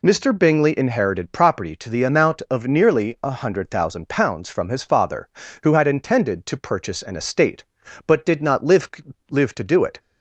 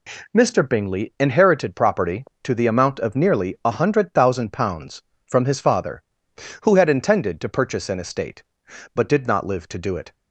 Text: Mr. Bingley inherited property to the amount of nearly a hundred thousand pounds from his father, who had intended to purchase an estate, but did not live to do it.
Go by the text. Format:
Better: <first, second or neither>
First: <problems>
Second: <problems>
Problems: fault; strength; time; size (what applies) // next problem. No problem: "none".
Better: second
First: says "live" twice; at 9.3 s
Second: none